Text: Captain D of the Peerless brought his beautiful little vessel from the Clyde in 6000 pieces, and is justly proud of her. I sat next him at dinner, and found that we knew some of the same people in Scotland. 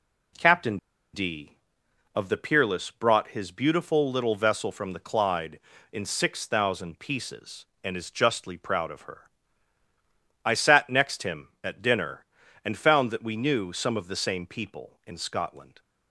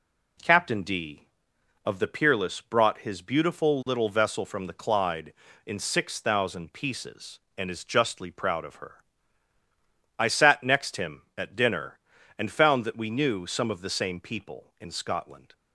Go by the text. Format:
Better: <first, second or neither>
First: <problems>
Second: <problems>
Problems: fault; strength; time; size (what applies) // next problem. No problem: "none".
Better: second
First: pauses between "Captain" and "D"; at 0.7 s; 0.36 s long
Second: none